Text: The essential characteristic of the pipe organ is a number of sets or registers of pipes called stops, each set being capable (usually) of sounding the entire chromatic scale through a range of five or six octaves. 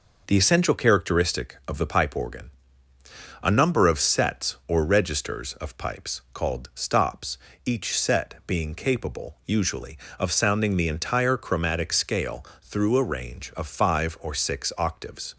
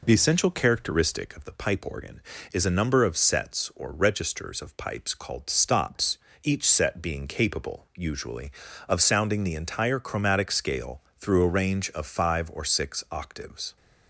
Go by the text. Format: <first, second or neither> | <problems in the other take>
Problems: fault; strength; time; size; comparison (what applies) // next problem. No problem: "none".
second | skips "is"; at 2.9 s // pauses between "scale" and "through"; slight; at 12.4 s; 0.16 s long; slight in the second